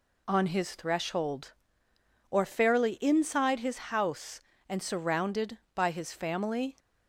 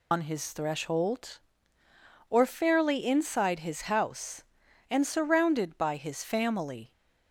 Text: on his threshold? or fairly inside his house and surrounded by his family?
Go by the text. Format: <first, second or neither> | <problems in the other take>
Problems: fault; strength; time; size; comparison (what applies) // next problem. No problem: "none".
first | loses the start of "on"; at 0.1 s; 85 ms